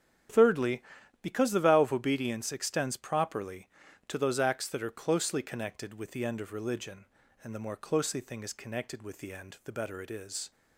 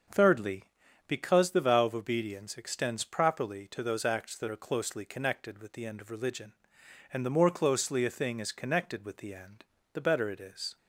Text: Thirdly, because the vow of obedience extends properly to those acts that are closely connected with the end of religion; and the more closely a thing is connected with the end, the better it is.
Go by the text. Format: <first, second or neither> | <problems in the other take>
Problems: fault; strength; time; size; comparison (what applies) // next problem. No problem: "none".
second | starts louder than the rest; strong; until 1.7 s; 9 dB; also in the second // skips "a"; at 8.1 s